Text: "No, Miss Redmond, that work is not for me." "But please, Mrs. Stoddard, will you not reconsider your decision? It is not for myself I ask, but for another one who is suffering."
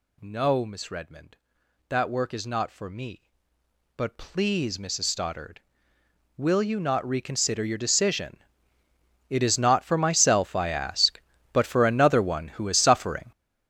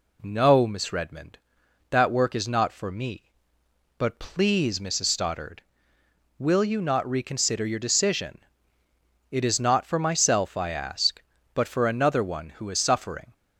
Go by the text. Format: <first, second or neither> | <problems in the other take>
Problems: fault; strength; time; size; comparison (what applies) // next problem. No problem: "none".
second | gets louder; strong; throughout; 13 dB